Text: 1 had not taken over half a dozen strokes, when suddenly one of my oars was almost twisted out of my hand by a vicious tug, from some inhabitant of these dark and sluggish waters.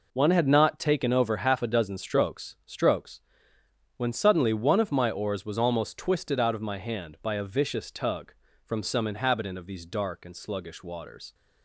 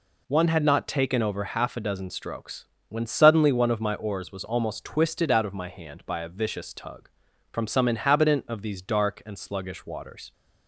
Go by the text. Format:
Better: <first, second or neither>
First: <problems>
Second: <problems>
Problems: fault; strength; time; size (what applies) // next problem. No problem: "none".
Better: second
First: says "strokes" twice; at 2.6 s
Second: none